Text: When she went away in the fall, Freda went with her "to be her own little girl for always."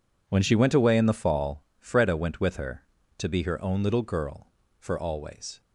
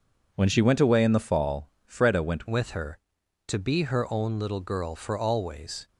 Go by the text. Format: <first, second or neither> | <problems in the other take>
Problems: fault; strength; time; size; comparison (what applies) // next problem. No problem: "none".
first | changes voice at "with"; from 2.4 s on; 3.4 s long